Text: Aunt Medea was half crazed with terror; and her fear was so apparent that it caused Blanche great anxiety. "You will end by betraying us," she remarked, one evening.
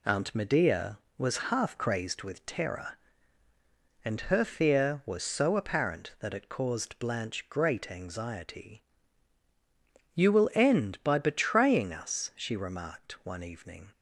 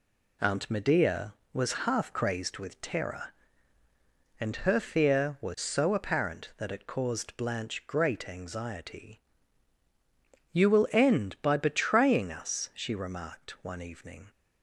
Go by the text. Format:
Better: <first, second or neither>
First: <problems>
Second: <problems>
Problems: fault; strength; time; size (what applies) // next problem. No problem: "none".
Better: neither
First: none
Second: none